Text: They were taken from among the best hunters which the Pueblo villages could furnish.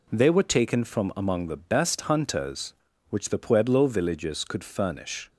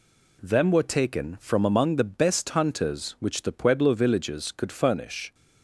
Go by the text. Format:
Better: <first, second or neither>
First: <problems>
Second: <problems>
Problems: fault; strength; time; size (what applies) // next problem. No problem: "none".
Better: first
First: none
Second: says "Them" for "They"; at 0.4 s